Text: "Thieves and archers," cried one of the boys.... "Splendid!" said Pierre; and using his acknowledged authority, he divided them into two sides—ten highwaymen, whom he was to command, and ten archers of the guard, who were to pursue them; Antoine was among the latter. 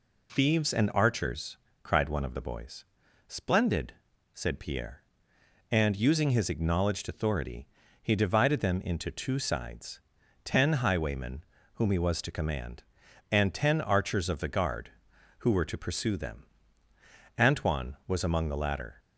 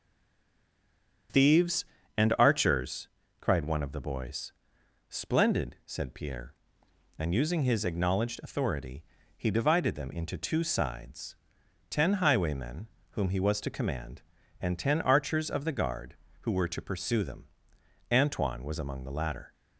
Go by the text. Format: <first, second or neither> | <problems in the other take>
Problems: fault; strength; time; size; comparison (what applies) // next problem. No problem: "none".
first | stays silent before the first word; noticeable; until 1.2 s; 1.2 s long // starts louder than the rest; strong; until 2.6 s; 7.5 dB